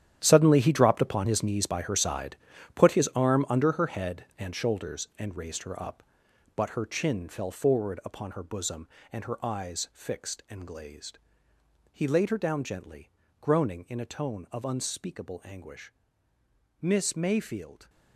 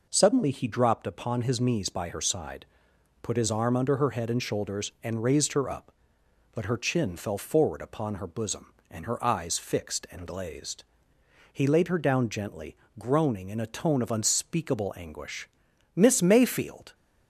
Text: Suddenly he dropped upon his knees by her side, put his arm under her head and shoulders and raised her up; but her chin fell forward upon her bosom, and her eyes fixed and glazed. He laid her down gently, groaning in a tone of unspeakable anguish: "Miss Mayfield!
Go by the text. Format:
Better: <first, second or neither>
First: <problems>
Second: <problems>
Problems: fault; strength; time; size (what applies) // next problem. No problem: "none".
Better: second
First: gets quieter; strong; throughout; 13.5 dB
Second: none